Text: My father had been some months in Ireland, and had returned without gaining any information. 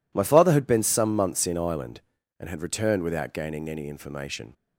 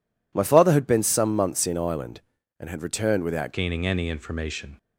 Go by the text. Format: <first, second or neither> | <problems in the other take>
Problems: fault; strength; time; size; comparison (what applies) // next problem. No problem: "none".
first | changes voice at "gaining"; from 3.5 s on; 1.2 s long